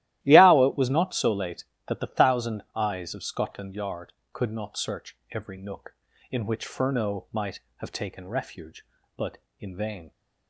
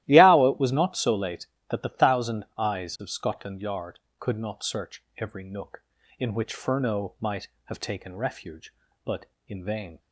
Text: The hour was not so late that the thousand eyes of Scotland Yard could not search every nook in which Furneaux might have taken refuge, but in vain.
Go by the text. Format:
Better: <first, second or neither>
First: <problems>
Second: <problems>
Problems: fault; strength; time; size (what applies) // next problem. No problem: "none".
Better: neither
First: starts louder than the rest; strong; until 1.2 s; 15 dB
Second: starts louder than the rest; strong; until 1.0 s; 15 dB